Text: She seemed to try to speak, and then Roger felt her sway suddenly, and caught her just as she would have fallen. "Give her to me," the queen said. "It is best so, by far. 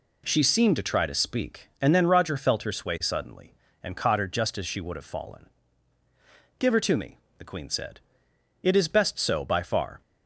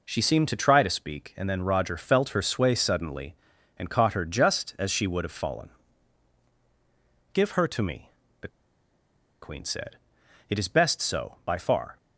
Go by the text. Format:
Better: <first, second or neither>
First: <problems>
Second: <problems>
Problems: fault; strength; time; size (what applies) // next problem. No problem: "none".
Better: first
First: none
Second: pauses between "the" and "queen"; noticeable; at 8.4 s; 0.94 s long